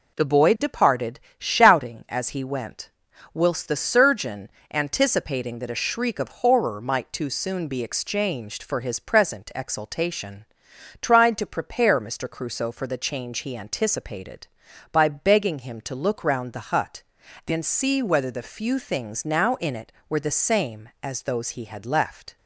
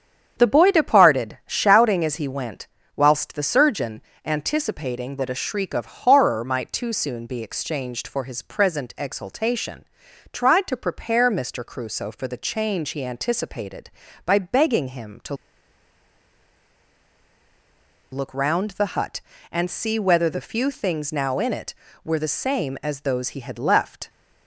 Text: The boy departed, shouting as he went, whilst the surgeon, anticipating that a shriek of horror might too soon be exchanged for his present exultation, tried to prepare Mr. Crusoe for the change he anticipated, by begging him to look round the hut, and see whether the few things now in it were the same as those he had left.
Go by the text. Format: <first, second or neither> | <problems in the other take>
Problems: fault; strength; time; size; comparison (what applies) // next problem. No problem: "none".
first | starts louder than the rest; strong; until 1.3 s; 8 dB // pauses between "to" and "look"; strong; at 15.3 s; 2.7 s long